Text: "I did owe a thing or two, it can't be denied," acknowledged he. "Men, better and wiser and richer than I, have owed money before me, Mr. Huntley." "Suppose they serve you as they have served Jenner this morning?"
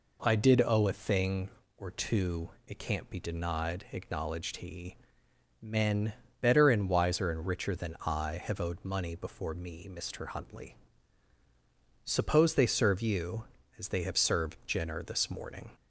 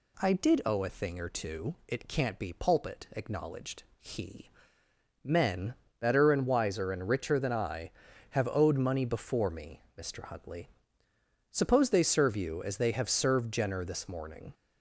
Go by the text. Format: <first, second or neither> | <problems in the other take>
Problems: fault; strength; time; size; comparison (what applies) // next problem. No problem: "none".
first | says "pulpit" for "denied"; at 2.5 s // pauses between "acknowledged" and "he"; slight; at 3.8 s; 0.16 s long